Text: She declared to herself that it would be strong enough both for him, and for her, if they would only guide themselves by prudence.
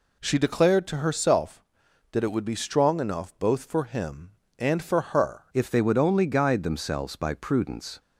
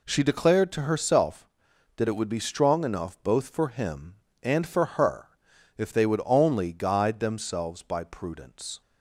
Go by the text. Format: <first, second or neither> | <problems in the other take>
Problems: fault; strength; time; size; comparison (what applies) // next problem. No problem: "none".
second | changes voice at "if"; from 5.5 s on; 2.4 s long